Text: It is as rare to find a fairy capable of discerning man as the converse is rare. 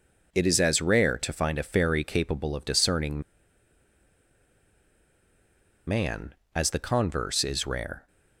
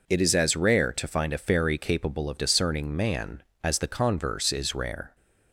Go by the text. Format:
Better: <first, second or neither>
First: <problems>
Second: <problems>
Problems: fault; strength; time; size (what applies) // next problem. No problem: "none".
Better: second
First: pauses between "discerning" and "man"; strong; at 3.2 s; 2.6 s long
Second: none